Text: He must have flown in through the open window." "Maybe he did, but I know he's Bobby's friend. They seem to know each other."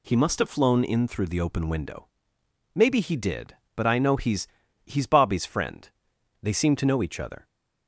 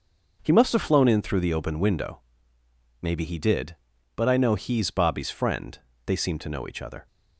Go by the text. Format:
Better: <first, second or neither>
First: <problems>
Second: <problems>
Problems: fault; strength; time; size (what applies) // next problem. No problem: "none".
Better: second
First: says "he's" twice; at 4.8 s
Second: none